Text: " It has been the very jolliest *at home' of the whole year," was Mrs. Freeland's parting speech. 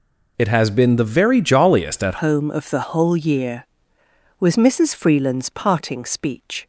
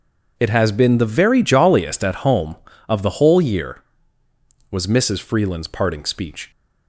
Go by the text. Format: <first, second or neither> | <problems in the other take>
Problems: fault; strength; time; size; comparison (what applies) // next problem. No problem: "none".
second | changes voice at "home"; from 2.2 s on; 4.4 s long